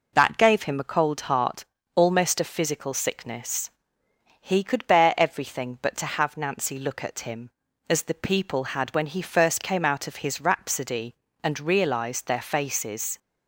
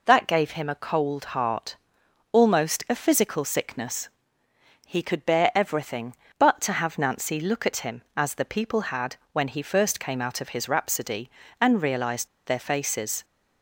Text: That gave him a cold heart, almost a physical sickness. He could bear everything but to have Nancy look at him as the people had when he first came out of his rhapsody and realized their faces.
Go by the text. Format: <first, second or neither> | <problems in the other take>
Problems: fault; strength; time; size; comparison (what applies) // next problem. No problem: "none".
first | pauses between "had" and "when"; slight; at 9.1 s; 0.18 s long // pauses between "realized" and "their"; slight; at 12.2 s; 0.20 s long